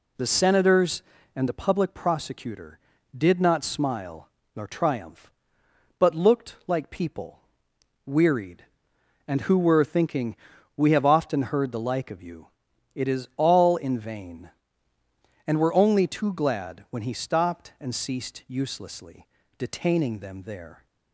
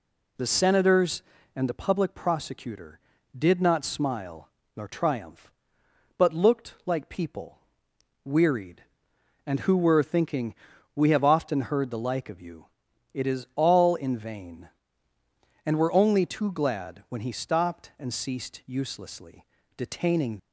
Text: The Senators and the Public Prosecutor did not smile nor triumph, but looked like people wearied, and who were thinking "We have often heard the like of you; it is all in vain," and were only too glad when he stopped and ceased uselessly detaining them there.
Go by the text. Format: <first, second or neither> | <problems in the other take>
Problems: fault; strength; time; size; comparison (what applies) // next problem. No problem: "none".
first | pauses between "smile" and "nor"; slight; at 4.5 s; 0.26 s long; slight in the first // pauses between "people" and "wearied"; noticeable; at 7.6 s; 0.64 s long; noticeable in the first // pauses between "thinking" and "We"; at 10.5 s; 0.40 s long; also in the first // pauses between "uselessly" and "detaining"; slight; at 19.4 s; 0.32 s long; slight in the first // stops before "them there"; at 20.3 s